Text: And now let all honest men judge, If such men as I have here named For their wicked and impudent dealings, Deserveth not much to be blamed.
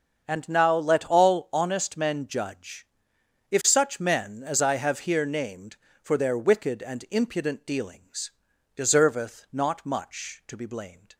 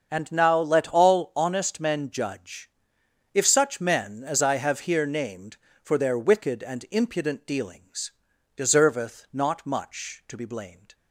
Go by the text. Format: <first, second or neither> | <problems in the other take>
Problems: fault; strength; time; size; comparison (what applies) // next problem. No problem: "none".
neither | starts louder than the rest; the same in both